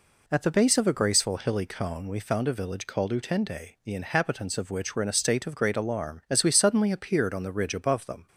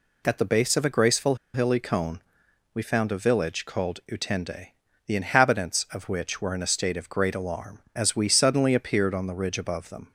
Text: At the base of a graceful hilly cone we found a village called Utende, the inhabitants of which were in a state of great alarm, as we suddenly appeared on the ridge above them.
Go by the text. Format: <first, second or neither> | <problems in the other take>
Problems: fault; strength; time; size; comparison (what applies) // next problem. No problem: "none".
first | pauses between "graceful" and "hilly"; slight; at 1.3 s; 0.18 s long // pauses between "cone" and "we"; noticeable; at 2.2 s; 0.52 s long